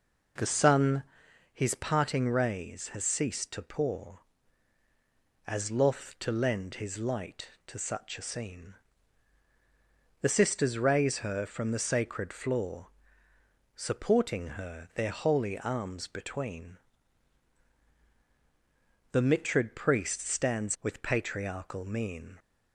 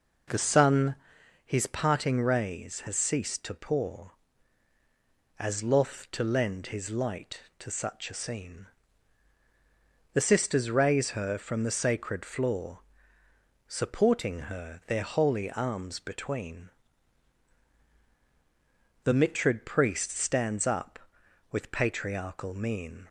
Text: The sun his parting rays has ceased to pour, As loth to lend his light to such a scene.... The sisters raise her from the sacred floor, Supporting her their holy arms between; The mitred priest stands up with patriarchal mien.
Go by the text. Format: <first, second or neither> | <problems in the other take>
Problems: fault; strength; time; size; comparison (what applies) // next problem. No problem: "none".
second | pauses between "sun" and "his"; noticeable; at 1.0 s; 0.48 s long; noticeable in the second // skips "up"; at 20.7 s